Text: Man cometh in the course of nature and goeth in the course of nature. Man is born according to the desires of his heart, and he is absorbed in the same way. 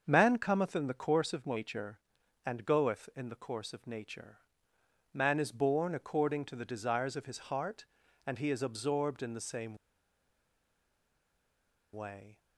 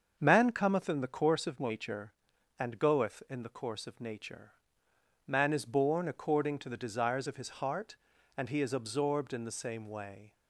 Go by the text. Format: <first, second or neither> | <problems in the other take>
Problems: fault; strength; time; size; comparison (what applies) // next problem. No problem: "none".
second | starts louder than the rest; until 1.0 s; 6.5 dB; also in the second // pauses between "same" and "way"; strong; at 9.7 s; 2.1 s long